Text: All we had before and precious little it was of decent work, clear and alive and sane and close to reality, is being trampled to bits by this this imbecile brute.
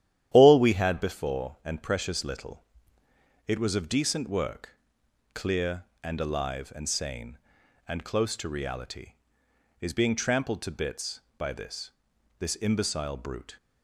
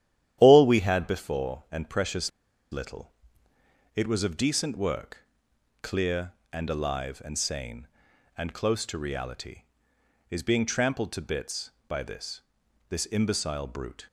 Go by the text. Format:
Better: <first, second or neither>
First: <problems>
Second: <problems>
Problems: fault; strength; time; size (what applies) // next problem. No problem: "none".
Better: first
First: starts louder than the rest; strong; until 1.3 s; 11 dB // pauses between "little" and "it"; noticeable; at 2.6 s; 0.84 s long // pauses between "this" and "this"; noticeable; at 11.9 s; 0.48 s long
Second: starts louder than the rest; strong; until 1.4 s; 11 dB // pauses between "precious" and "little"; at 2.3 s; 0.42 s long // pauses between "little" and "it"; noticeable; at 3.1 s; 0.84 s long // pauses between "this" and "this"; noticeable; at 12.4 s; 0.48 s long